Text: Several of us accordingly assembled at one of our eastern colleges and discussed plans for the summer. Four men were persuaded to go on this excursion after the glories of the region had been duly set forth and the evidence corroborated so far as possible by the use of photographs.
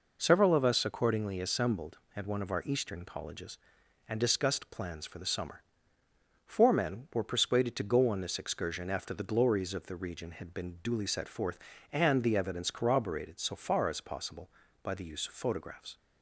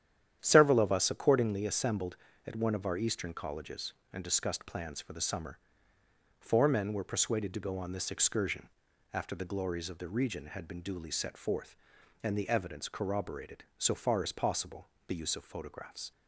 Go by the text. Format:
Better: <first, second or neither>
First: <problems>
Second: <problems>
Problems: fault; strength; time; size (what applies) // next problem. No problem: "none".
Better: first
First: none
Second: starts louder than the rest; strong; until 1.4 s; 10 dB // pauses between "excursion" and "after"; at 8.6 s; 0.42 s long // skips "by"; at 14.9 s